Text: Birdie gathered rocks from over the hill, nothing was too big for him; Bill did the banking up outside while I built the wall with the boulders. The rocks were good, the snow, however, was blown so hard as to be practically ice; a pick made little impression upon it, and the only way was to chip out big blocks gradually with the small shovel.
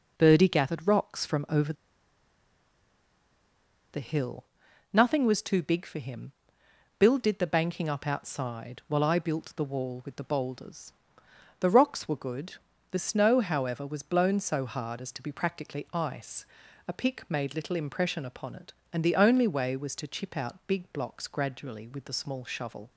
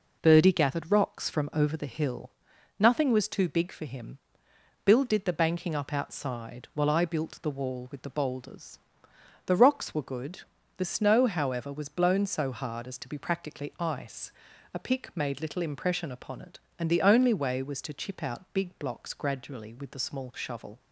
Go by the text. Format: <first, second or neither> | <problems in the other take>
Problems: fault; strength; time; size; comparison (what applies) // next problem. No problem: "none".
second | pauses between "over" and "the"; strong; at 1.7 s; 2.1 s long